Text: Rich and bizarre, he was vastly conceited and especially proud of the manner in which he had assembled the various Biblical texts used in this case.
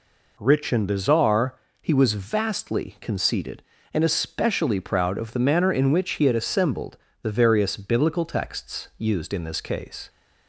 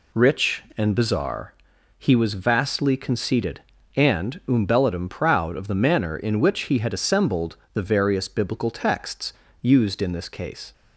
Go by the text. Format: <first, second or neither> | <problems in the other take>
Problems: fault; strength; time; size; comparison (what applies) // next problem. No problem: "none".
first | says "umbellatum" for "especially"; at 4.4 s // pauses between "assembled" and "the"; slight; at 7.5 s; 0.18 s long; slight in the first // pauses between "texts" and "used"; slight; at 9.3 s; 0.30 s long